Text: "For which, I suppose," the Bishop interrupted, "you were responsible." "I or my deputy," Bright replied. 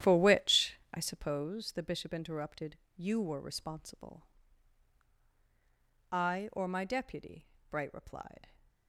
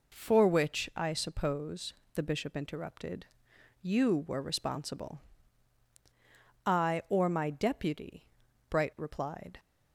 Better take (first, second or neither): second